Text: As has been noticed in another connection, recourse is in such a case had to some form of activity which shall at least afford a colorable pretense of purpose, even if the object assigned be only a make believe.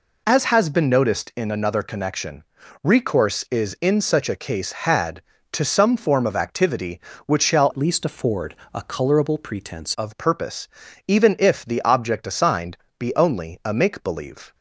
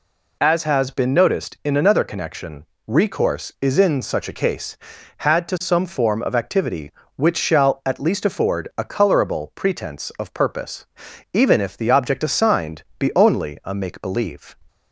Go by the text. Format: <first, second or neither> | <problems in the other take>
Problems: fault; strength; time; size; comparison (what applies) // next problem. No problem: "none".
second | changes voice from "at" to "pretense"; from 7.7 to 9.9 s; 2.2 s long // pauses between "afford" and "a"; slight; at 8.5 s; 0.18 s long // pauses between "assigned" and "be"; slight; at 12.7 s; 0.20 s long; slight in the second